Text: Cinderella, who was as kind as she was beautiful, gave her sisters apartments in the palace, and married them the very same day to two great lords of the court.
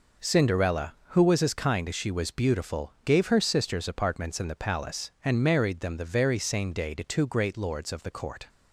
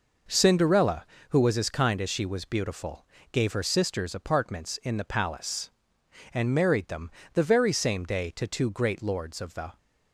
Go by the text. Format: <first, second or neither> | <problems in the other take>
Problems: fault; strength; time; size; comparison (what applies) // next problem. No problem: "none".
first | pauses between "them" and "the"; slight; at 7.0 s; 0.24 s long // stops before "court"; at 9.7 s